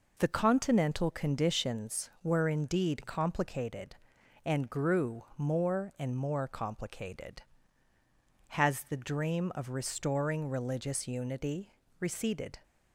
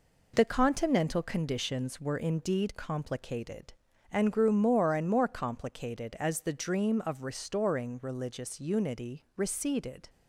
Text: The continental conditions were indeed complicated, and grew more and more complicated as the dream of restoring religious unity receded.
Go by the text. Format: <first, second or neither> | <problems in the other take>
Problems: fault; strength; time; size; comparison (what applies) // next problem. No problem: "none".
second | says "has" for "as"; at 8.5 s // pauses between "unity" and "receded"; slight; at 11.7 s; 0.28 s long